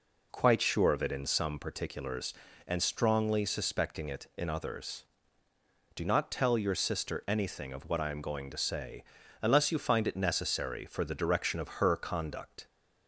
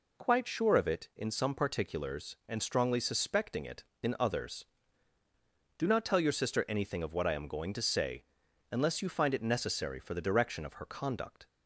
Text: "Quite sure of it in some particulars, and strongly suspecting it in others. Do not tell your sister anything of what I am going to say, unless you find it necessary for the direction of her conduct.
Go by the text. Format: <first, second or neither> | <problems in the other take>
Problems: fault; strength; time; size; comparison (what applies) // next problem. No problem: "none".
neither | none